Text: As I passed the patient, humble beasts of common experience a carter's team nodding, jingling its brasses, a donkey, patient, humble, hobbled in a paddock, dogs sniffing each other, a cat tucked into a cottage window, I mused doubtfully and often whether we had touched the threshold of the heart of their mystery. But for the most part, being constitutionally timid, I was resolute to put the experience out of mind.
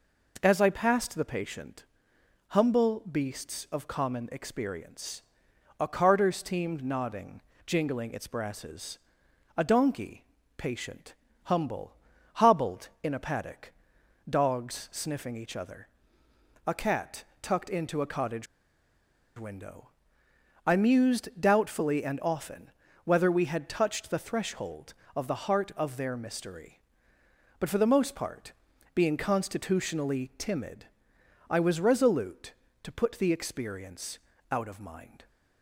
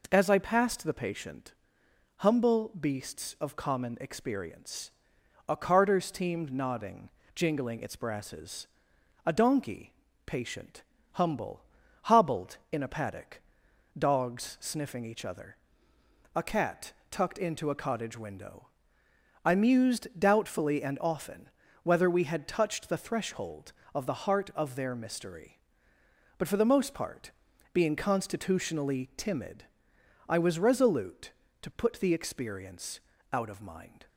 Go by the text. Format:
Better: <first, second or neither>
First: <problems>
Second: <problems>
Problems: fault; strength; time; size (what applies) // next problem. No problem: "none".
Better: second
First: pauses between "experience" and "a"; noticeable; at 5.2 s; 0.56 s long // pauses between "cat" and "tucked"; slight; at 17.2 s; 0.18 s long // pauses between "cottage" and "window"; noticeable; at 18.4 s; 0.92 s long // pauses between "often" and "whether"; slight; at 22.7 s; 0.34 s long // pauses between "experience" and "out"; slight; at 34.1 s; 0.32 s long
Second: pauses between "experience" and "a"; noticeable; at 4.9 s; 0.56 s long // pauses between "cat" and "tucked"; slight; at 16.9 s; 0.18 s long // pauses between "often" and "whether"; slight; at 21.4 s; 0.34 s long // pauses between "experience" and "out"; slight; at 32.9 s; 0.32 s long